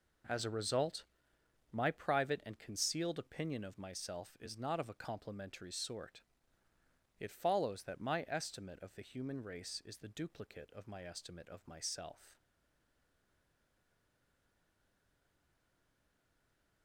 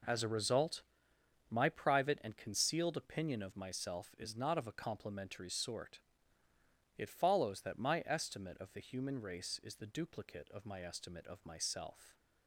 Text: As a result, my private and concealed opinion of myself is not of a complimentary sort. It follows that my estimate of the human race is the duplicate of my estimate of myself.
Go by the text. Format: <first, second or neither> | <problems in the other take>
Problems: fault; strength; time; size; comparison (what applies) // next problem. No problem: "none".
second | stays silent after the last word; strong; from 12.3 s on; 4.5 s long